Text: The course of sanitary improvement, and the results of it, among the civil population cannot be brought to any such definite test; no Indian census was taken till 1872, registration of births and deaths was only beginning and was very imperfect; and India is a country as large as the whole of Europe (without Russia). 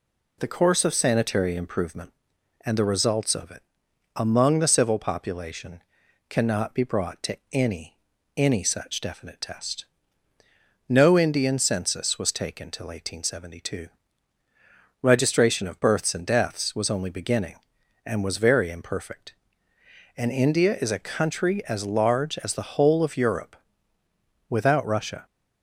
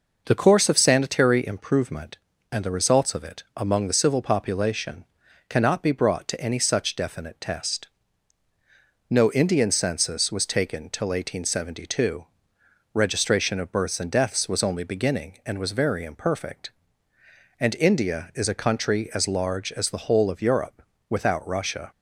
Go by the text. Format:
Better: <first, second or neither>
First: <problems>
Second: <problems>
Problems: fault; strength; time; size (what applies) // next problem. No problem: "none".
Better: second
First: pauses between "population" and "cannot"; noticeable; at 5.8 s; 0.48 s long // says "any" twice; at 8.3 s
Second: pauses between "population" and "cannot"; at 5.0 s; 0.44 s long